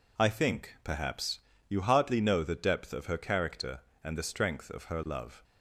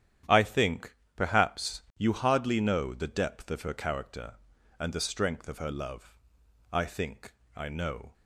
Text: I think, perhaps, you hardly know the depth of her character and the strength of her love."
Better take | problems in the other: first | starts louder than the rest; strong; until 1.5 s; 10 dB // goes on to say "I think I know"; from 6.7 s on; 1.4 s long

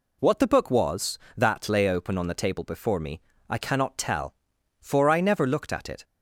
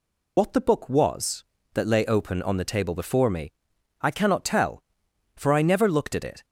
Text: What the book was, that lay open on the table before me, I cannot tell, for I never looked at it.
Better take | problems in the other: first | loses the start of "What"; at 0.3 s; 45 ms

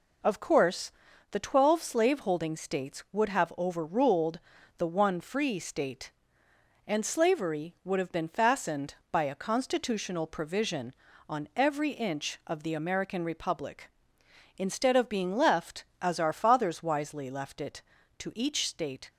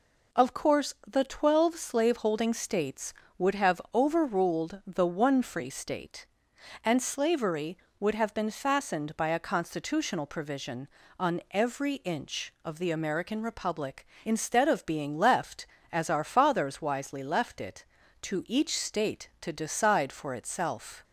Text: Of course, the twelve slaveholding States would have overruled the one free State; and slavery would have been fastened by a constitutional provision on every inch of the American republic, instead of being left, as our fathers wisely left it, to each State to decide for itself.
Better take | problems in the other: second | pauses between "overruled" and "the"; at 4.3 s; 0.38 s long // stops before "to decide for itself"; at 19.0 s

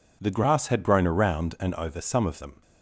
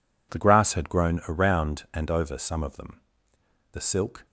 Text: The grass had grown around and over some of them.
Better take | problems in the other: first | goes on to say "The silk"; from 3.7 s on; 0.54 s long

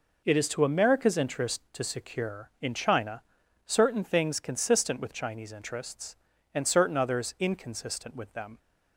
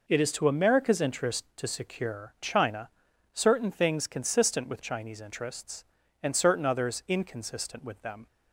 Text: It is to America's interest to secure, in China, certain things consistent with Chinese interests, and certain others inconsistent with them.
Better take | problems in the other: first | skips "in"; at 2.3 s

